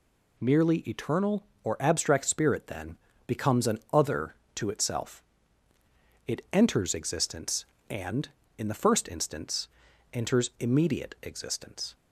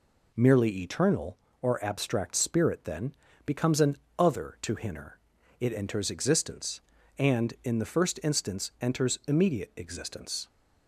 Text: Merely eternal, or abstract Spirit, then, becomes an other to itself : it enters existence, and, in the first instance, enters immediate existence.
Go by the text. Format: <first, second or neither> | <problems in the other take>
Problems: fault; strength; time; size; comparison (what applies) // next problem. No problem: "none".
first | pauses between "an" and "other"; slight; at 3.9 s; 0.20 s long // says "hinner" for "itself"; at 4.7 s